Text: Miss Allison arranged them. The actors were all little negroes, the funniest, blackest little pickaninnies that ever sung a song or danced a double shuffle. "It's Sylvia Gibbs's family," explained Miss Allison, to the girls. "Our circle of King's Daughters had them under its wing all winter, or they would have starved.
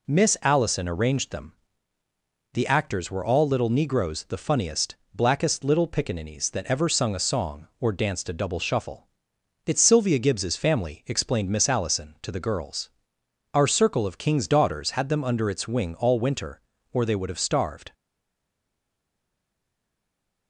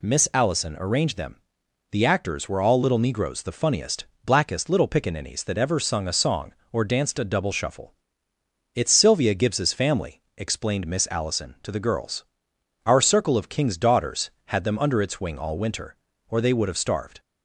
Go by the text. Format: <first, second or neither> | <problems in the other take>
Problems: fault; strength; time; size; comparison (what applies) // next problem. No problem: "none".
second | stays silent after the last word; strong; from 17.9 s on; 2.5 s long